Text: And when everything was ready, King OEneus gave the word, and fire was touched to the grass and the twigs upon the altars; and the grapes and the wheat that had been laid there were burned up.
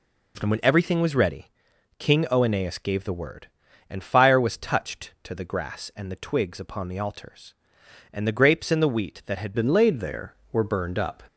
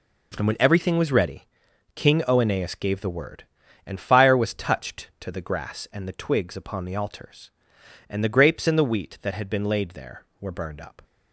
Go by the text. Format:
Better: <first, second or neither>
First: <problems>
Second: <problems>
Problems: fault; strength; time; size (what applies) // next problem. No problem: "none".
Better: second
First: changes voice at "been"; from 9.5 s on; 1.7 s long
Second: none